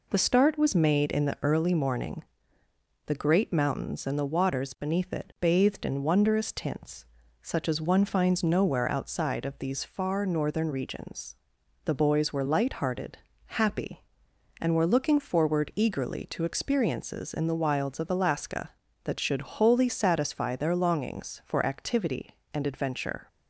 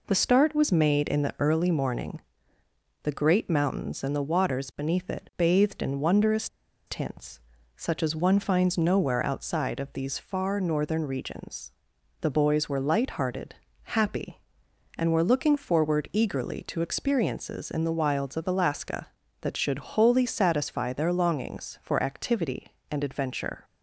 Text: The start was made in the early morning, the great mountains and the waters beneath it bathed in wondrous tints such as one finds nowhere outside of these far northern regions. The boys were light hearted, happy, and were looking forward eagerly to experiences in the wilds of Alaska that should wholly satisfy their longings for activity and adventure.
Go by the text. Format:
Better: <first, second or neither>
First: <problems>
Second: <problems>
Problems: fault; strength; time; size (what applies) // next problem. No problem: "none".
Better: first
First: pauses between "tints" and "such"; at 7.0 s; 0.38 s long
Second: pauses between "wondrous" and "tints"; at 6.4 s; 0.40 s long // pauses between "tints" and "such"; at 7.3 s; 0.38 s long